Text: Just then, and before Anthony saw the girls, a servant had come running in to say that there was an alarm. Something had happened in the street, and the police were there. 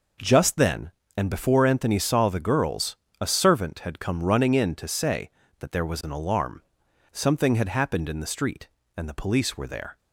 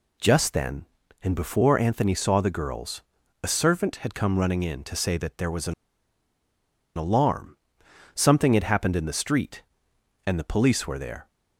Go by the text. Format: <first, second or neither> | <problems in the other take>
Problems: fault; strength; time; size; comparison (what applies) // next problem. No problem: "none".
first | pauses between "an" and "alarm"; at 5.7 s; 1.2 s long